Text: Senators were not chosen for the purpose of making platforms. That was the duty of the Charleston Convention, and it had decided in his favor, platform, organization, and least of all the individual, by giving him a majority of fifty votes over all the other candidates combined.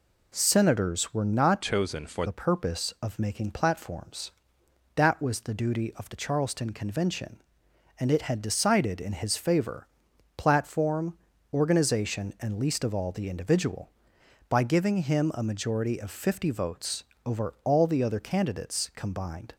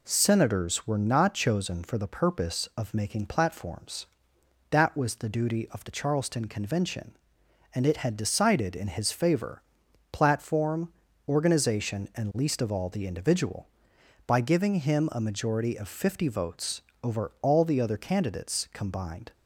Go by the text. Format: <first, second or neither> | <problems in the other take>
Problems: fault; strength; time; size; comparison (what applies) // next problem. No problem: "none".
second | changes voice from "chosen" to "for"; from 1.6 to 2.2 s; 0.6 s long // pauses between "votes" and "over"; slight; at 17.0 s; 0.22 s long; slight in the second